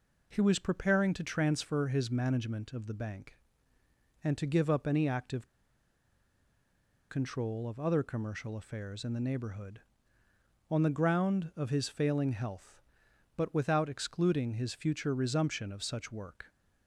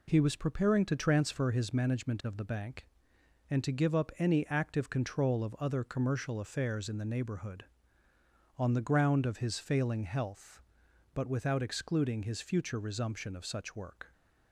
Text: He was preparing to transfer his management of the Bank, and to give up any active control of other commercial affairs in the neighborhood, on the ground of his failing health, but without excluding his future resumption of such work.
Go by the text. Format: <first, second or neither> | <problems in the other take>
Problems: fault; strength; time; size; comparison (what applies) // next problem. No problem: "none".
second | pauses between "active" and "control"; strong; at 5.4 s; 1.6 s long